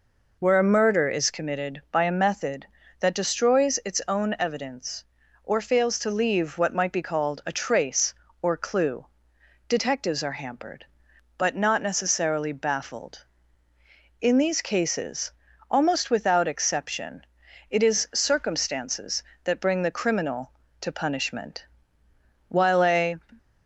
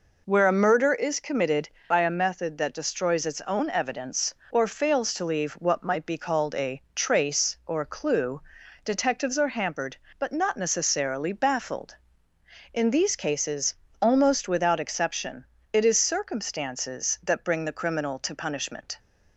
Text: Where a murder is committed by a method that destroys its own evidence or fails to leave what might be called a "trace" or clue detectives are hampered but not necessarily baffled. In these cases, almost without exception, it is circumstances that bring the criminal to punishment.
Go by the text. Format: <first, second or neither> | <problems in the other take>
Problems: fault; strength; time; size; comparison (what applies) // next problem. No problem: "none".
second | pauses between "clue" and "detectives"; noticeable; at 9.0 s; 0.62 s long; also in the second // goes on to say "While a"; noticeable; from 22.4 s on; 0.70 s long